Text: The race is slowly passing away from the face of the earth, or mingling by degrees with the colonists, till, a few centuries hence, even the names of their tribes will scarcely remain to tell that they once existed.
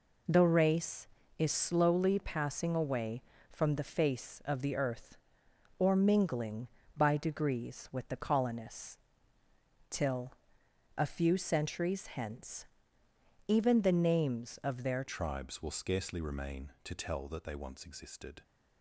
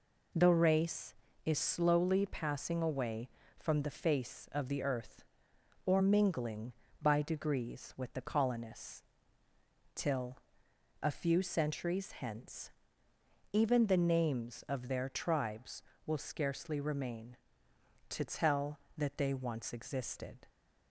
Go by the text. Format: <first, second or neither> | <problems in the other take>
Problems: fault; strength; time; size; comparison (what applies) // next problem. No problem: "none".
second | changes voice at "tribes"; from 15.0 s on; 3.4 s long